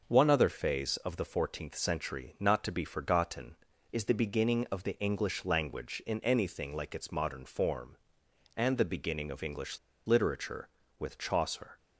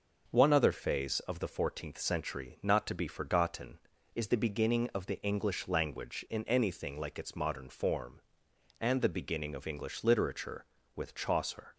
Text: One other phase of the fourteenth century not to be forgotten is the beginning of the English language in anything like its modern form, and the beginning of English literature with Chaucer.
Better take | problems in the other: second | pauses between "English" and "literature"; slight; at 9.7 s; 0.28 s long

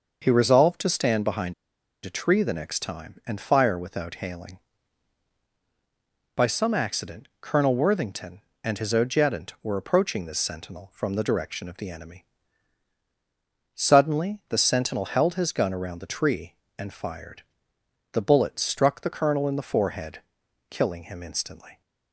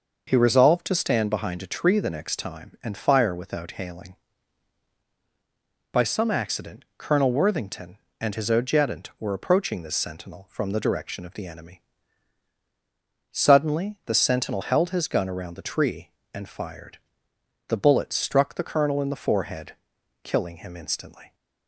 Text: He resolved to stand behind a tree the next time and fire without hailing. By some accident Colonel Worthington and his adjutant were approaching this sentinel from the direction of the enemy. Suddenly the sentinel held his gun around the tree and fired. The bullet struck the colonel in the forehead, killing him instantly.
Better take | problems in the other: second | pauses between "behind" and "a"; noticeable; at 1.5 s; 0.51 s long

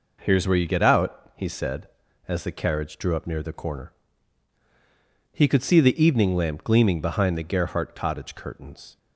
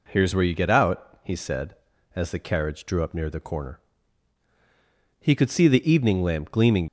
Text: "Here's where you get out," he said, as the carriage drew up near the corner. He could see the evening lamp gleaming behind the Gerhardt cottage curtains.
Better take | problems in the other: first | stops before "behind the Gerhardt cottage curtains"; at 6.8 s

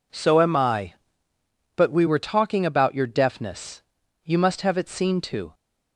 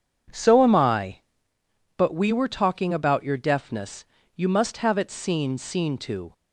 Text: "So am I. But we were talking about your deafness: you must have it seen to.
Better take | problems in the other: first | says "seen" twice; at 5.5 s

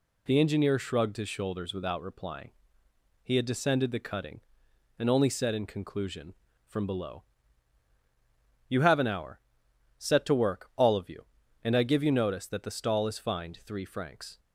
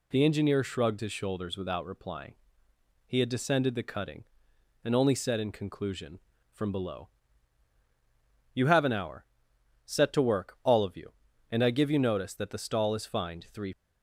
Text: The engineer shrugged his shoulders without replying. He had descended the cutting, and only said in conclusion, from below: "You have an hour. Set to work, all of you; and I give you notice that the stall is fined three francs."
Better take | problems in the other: first | stops before "francs"; at 13.7 s

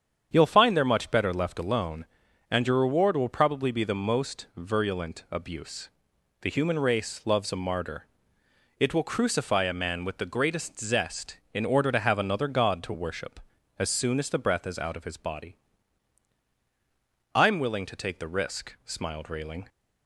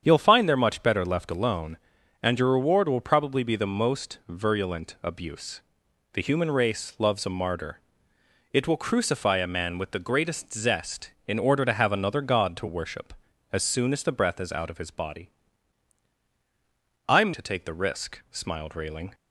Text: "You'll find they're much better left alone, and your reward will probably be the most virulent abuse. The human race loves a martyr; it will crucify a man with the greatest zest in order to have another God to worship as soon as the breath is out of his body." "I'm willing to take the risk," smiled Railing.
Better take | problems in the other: first | starts louder than the rest; strong; until 1.0 s; 8 dB; strong in the first // skips "willing"; at 17.3 s

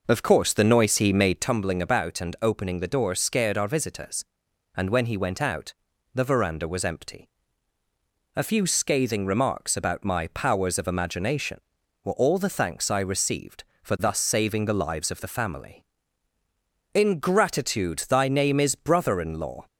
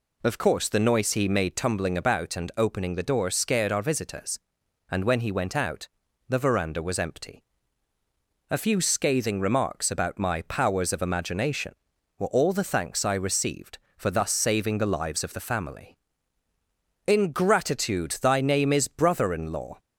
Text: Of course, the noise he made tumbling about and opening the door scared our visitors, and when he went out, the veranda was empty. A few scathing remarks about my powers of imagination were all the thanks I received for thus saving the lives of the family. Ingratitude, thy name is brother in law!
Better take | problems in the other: second | starts louder than the rest; noticeable; until 1.5 s; 5.5 dB

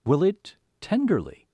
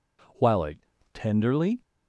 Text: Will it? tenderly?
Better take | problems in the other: first | says "While" for "Will"; at 0.3 s

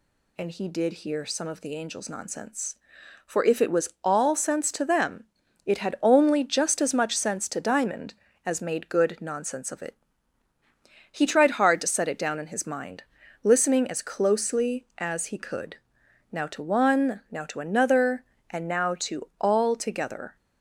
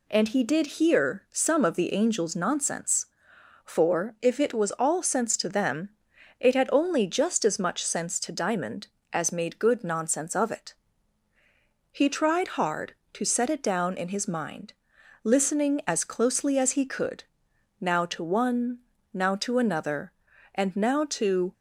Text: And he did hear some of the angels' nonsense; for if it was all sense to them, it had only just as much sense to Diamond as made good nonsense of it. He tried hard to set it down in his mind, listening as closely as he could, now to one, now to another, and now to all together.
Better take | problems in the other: first | stops before "all together"; at 21.5 s

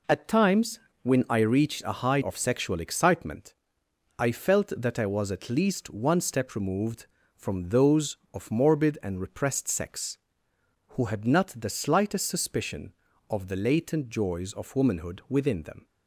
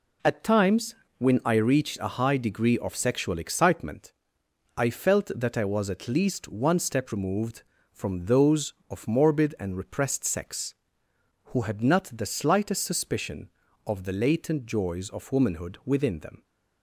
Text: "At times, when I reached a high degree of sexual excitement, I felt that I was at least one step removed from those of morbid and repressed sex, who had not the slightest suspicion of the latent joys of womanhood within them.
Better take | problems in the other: second | skips "degree"; at 2.2 s

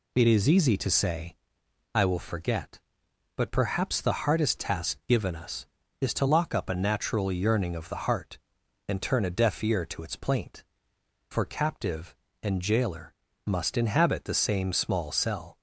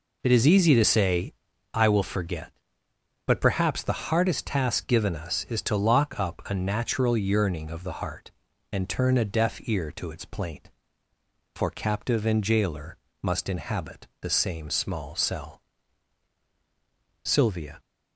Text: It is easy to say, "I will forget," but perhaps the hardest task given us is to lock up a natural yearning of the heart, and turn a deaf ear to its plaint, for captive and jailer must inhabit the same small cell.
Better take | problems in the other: first | pauses between "jailer" and "must"; slight; at 12.9 s; 0.24 s long; slight in the first // goes on to say "Sylvia"; from 17.2 s on; 0.56 s long

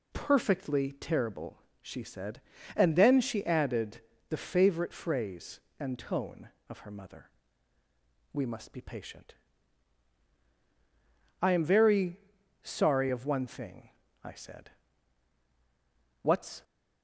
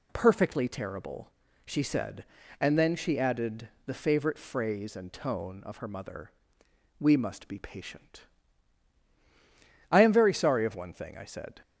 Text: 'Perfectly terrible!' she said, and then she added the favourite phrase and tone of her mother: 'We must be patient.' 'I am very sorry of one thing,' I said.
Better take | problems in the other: second | pauses between "added" and "the"; slight; at 4.0 s; 0.28 s long; slight in the second // pauses between "very" and "sorry"; at 12.1 s; 0.42 s long // goes on to say "What's"; slight; from 16.2 s on; 0.42 s long

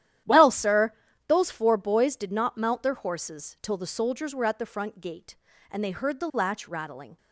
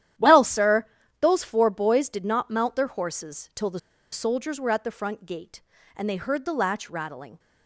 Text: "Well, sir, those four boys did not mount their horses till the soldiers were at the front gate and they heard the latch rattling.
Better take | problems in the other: first | starts louder than the rest; strong; until 1.5 s; 11.5 dB; strong in the first // pauses between "the" and "soldiers"; slight; at 3.7 s; 0.33 s long

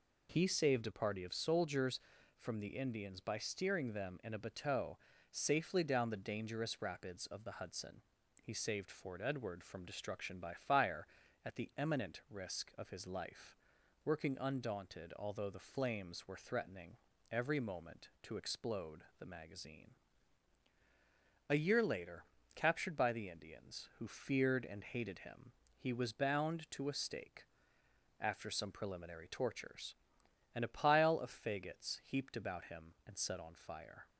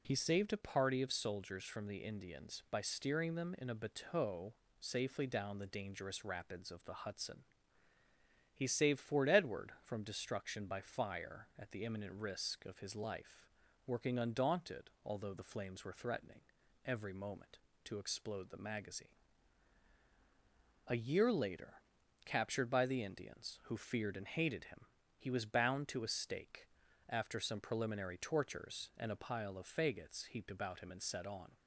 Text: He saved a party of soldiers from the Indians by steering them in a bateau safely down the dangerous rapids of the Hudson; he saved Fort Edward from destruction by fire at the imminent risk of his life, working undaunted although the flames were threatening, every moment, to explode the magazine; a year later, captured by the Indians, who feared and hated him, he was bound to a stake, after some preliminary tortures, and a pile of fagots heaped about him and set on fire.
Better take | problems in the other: first | pauses between "bateau" and "safely"; slight; at 4.5 s; 0.24 s long; slight in the first // stops before "fire"; at 31.5 s

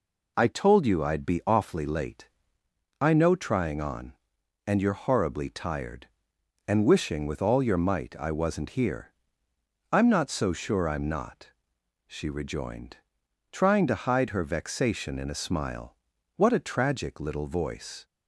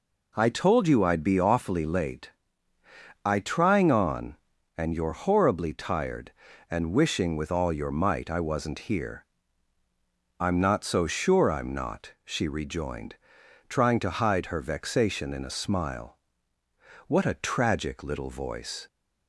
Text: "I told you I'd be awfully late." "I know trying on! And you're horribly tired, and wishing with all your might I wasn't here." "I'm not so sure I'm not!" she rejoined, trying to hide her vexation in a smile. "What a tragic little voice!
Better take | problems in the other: first | skips "know"; at 3.3 s

